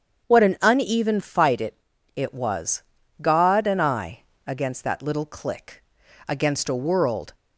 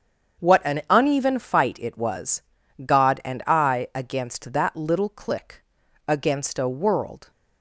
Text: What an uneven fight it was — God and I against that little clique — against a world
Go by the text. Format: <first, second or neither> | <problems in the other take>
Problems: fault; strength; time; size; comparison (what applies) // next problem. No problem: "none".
second | starts louder than the rest; strong; until 1.3 s; 7.5 dB; strong in the second // says "it" twice; at 2.1 s // pauses between "I" and "against"; slight; at 4.1 s; 0.26 s long